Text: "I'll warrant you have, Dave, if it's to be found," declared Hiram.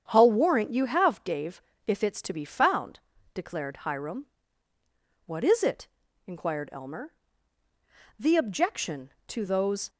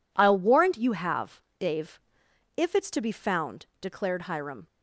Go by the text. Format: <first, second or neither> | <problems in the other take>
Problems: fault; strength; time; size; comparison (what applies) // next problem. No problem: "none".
second | starts louder than the rest; strong; until 1.0 s; 8 dB // goes on to say "What is it inquired Elmer The objection to those"; strong; from 5.2 s on; 4.6 s long